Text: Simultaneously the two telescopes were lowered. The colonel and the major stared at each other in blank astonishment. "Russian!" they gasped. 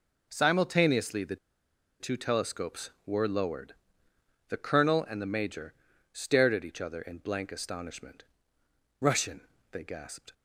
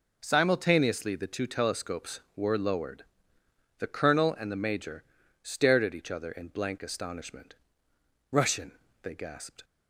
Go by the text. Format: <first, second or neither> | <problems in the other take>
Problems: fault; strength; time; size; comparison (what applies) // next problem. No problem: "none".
second | pauses between "the" and "two"; noticeable; at 1.3 s; 0.64 s long // pauses between "major" and "stared"; at 5.7 s; 0.40 s long; also in the second